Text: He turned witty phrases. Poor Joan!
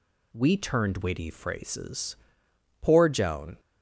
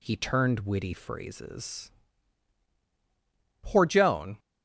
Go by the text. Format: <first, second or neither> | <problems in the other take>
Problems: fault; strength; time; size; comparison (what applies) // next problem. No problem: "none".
second | says "We" for "He"; at 0.3 s